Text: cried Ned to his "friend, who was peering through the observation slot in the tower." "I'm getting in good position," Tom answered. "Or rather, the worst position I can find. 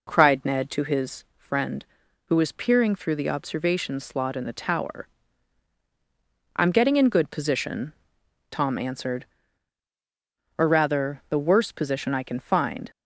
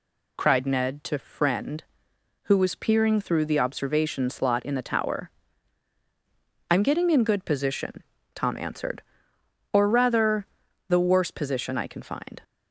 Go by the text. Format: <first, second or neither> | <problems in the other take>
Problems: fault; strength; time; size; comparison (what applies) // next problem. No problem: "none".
first | skips "his"; at 1.1 s